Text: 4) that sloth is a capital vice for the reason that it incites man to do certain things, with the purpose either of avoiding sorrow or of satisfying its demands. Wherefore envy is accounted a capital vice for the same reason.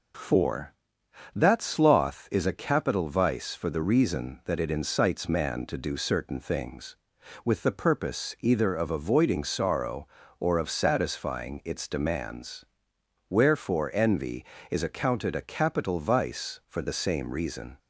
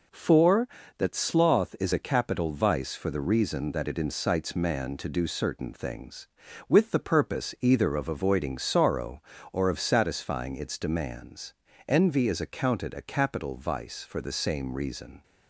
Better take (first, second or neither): first